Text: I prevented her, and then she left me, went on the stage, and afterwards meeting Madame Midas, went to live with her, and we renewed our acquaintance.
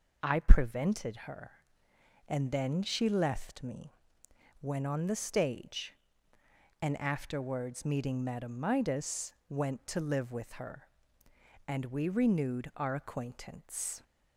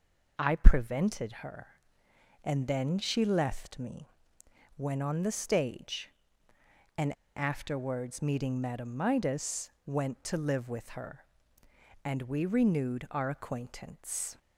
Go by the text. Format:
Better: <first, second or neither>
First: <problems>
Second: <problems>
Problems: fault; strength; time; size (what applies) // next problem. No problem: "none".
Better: first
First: none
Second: pauses between "and" and "afterwards"; slight; at 7.1 s; 0.21 s long